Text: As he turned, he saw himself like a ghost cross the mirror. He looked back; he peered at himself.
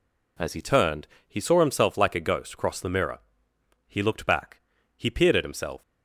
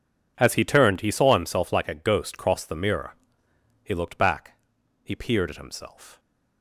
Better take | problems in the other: neither | none

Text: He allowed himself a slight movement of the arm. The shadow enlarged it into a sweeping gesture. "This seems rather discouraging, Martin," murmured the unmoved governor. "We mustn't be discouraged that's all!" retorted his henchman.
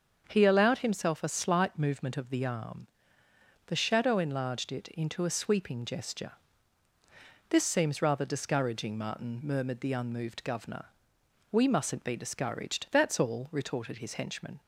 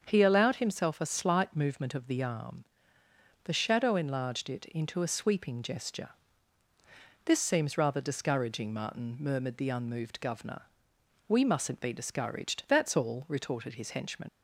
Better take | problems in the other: first | starts louder than the rest; until 1.0 s; 7 dB; also in the first // leaves "henchman" unfinished; at 14.2 s; 80 ms

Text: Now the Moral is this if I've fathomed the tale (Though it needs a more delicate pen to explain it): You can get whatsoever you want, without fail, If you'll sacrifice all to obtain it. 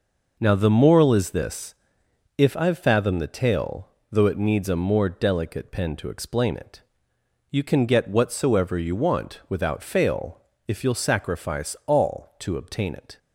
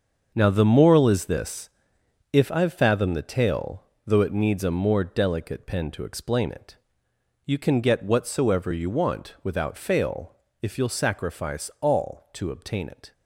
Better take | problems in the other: first | gets quieter; strong; throughout; 10.5 dB // pauses between "this" and "if"; noticeable; at 1.6 s; 0.64 s long; noticeable in the first

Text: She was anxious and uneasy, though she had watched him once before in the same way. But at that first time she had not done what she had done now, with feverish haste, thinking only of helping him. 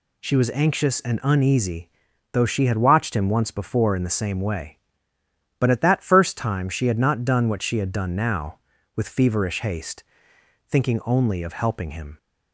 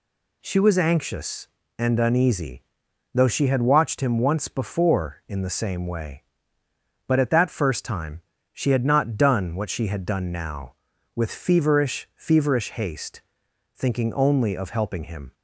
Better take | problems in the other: first | pauses between "time" and "she"; slight; at 8.2 s; 0.30 s long // says "feverish" twice; at 12.1 s

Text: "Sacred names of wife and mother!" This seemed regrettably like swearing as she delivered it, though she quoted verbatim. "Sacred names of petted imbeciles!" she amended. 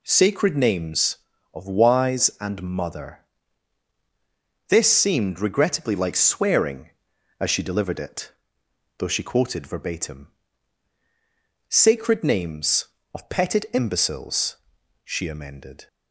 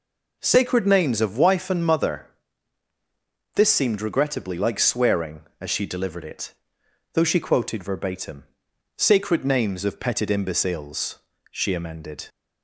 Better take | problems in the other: second | says "wise" for "wife"; at 1.6 s

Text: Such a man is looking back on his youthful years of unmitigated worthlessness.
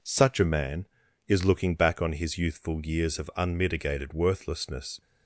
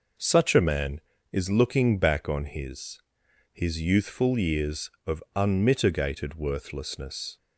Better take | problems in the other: first | says "his" twice; at 3.5 s

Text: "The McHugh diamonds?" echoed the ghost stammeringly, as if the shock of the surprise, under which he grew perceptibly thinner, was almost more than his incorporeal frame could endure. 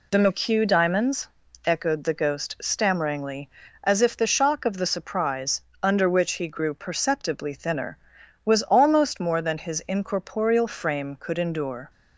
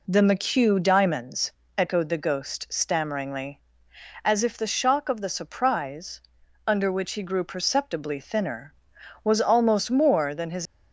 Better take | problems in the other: first | stops before "incorporeal frame could endure"; at 10.6 s

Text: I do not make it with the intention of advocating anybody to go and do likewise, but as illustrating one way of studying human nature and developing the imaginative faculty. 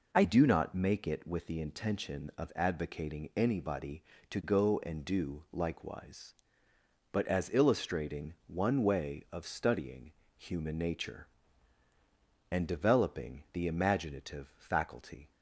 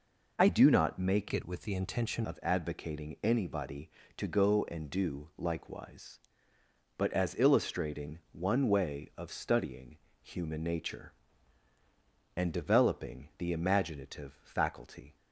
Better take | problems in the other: first | changes voice from "it" to "intention"; from 1.3 to 2.2 s; 0.9 s long // pauses between "studying" and "human"; slight; at 9.9 s; 0.26 s long; slight in the first

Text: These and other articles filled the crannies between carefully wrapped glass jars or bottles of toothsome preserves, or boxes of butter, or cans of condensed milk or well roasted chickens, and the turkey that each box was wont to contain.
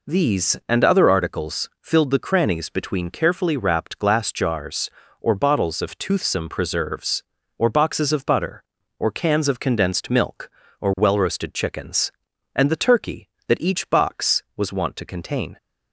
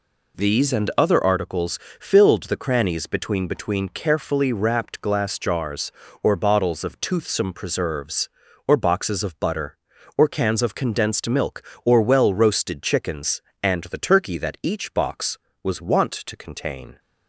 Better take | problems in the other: first | pauses between "articles" and "filled"; slight; at 1.7 s; 0.20 s long // says "between" twice; at 3.4 s

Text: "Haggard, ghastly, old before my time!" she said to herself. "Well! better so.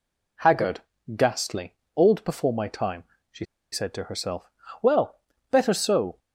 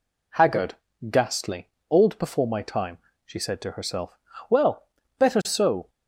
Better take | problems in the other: second | pauses between "she" and "said"; slight; at 3.4 s; 0.26 s long

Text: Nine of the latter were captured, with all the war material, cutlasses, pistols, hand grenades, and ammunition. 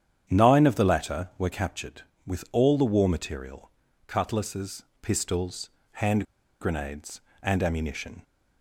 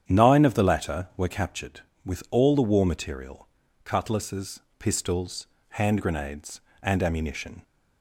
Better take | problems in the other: second | starts louder than the rest; strong; until 1.2 s; 9 dB; strong in the second // pauses between "hand" and "grenades"; slight; at 6.2 s; 0.36 s long

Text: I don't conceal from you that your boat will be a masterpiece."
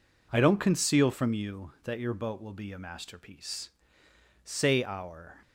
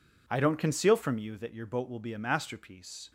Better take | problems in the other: second | goes on to say "Say our"; noticeable; from 4.4 s on; 0.94 s long

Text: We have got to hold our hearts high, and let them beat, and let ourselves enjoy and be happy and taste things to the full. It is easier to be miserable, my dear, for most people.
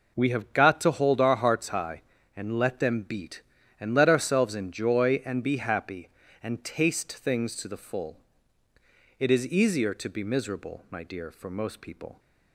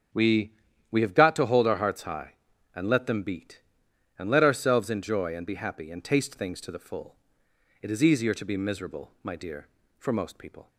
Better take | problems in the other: first | starts louder than the rest; strong; until 1.5 s; 9 dB // says "We" twice; at 0.9 s

